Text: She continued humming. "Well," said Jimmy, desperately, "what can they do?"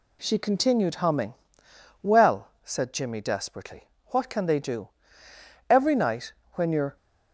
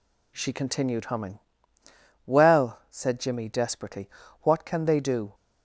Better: second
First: goes on to say "Every night when you're"; noticeable; from 5.6 s on; 1.2 s long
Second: none

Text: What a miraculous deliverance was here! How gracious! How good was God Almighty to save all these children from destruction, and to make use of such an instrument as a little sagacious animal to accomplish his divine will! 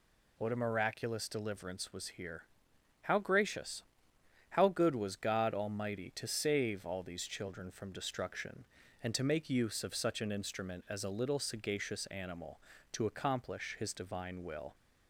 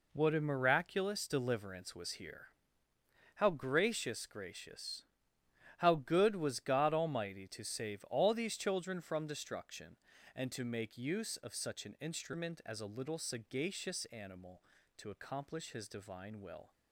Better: first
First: none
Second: says "gracious" twice; at 4.2 s

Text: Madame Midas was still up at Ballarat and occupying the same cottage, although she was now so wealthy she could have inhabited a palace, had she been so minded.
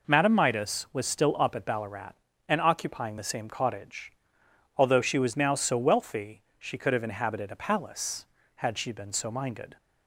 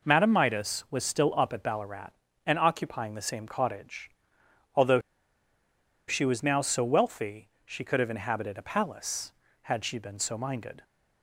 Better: first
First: pauses between "wealthy" and "she"; slight; at 6.4 s; 0.16 s long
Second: pauses between "although" and "she"; at 4.9 s; 1.0 s long // pauses between "wealthy" and "she"; slight; at 7.4 s; 0.16 s long

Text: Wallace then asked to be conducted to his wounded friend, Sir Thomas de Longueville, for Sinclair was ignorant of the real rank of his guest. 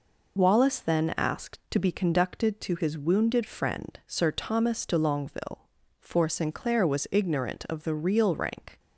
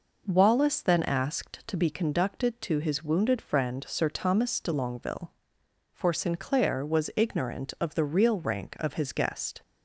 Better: second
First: stops before "of his guest"; at 8.7 s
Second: none

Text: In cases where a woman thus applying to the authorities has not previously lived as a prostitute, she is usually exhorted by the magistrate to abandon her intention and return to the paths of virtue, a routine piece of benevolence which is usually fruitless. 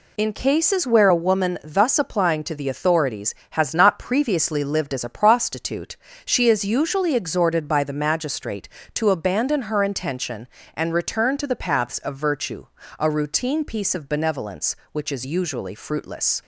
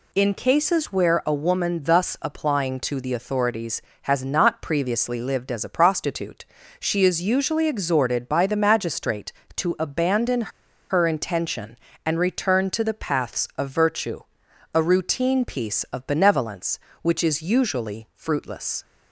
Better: first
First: none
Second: pauses between "abandon" and "her"; at 10.5 s; 0.39 s long

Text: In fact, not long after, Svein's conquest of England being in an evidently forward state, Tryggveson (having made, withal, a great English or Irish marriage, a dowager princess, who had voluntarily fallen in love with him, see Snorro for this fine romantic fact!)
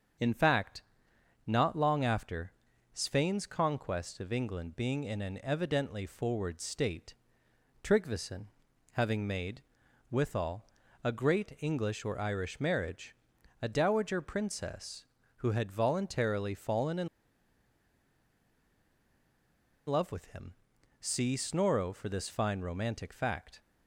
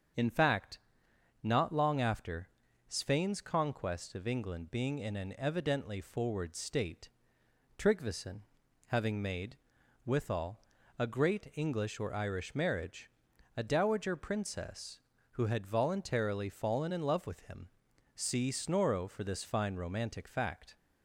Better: second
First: starts louder than the rest; until 1.8 s; 6.5 dB // pauses between "in" and "love"; strong; at 17.0 s; 2.8 s long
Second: starts louder than the rest; until 1.8 s; 6.5 dB

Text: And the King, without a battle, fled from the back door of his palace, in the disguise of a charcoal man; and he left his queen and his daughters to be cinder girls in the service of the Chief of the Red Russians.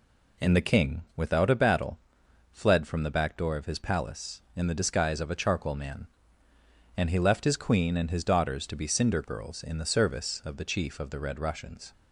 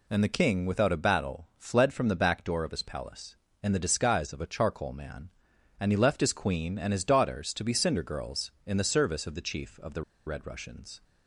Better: first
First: none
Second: pauses between "the" and "Red"; slight; at 10.0 s; 0.23 s long

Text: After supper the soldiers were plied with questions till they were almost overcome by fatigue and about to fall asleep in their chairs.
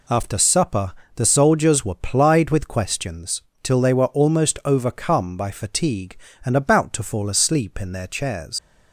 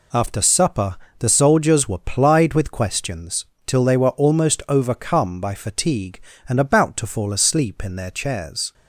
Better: second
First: pauses between "supper" and "the"; slight; at 0.9 s; 0.24 s long // pauses between "questions" and "till"; slight; at 3.4 s; 0.20 s long // leaves "chairs" unfinished; at 8.5 s; 110 ms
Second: pauses between "supper" and "the"; slight; at 0.9 s; 0.24 s long // pauses between "questions" and "till"; slight; at 3.4 s; 0.20 s long

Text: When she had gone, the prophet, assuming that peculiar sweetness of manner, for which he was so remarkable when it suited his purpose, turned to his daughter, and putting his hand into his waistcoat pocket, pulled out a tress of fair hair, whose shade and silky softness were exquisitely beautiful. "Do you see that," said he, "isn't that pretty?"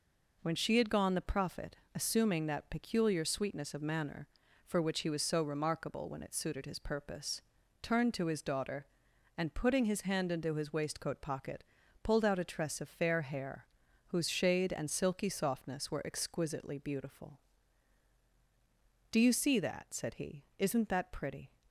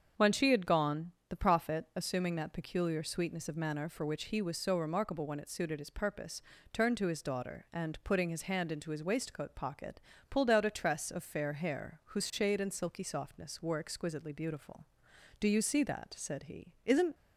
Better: first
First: none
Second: starts louder than the rest; strong; until 1.3 s; 7 dB // stops before "that pretty"; at 17.1 s

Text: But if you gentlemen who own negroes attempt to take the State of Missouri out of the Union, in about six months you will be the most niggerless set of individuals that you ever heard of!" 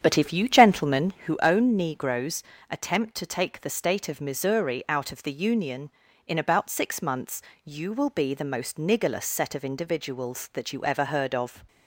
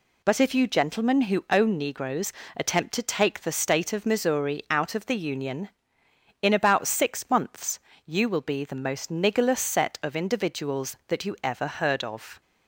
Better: second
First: starts louder than the rest; strong; until 1.4 s; 8.5 dB // pauses between "negroes" and "attempt"; slight; at 2.4 s; 0.28 s long // pauses between "months" and "you"; slight; at 7.4 s; 0.24 s long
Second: pauses between "negroes" and "attempt"; slight; at 2.3 s; 0.24 s long // pauses between "months" and "you"; slight; at 7.7 s; 0.26 s long

